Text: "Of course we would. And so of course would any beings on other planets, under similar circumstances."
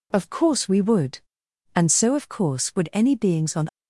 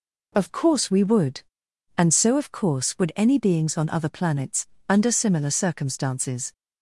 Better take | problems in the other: second | stops before "other planets under similar circumstances"; at 3.6 s

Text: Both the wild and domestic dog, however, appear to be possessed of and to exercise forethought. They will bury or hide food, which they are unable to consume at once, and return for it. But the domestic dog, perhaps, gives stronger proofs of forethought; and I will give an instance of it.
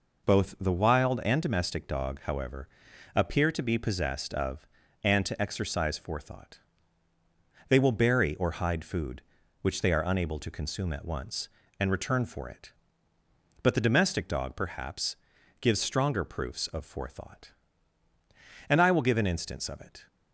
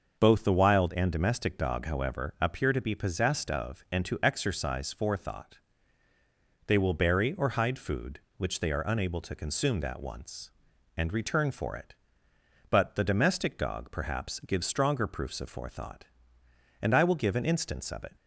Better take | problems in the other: first | starts louder than the rest; noticeable; until 1.2 s; 6 dB // says "that" for "at"; at 9.8 s

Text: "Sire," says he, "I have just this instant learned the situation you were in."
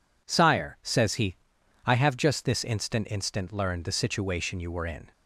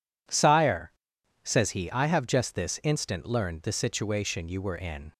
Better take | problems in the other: second | says "instant" twice; at 3.0 s

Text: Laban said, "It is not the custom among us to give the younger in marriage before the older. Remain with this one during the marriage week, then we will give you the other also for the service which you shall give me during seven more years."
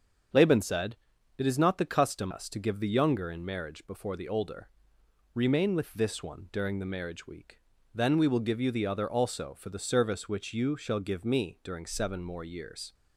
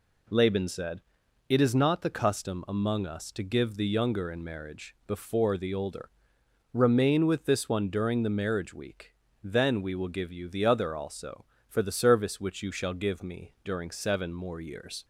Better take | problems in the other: second | starts louder than the rest; strong; until 1.7 s; 7.5 dB // skips "among"; at 2.3 s

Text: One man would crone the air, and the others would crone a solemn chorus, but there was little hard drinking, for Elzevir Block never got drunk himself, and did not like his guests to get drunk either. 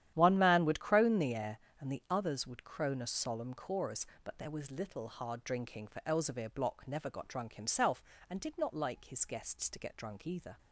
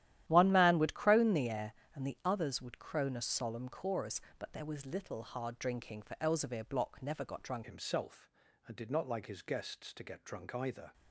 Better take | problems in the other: first | starts louder than the rest; strong; until 1.2 s; 12.5 dB; strong in the first // changes voice at "himself"; from 7.6 s on; 3.3 s long

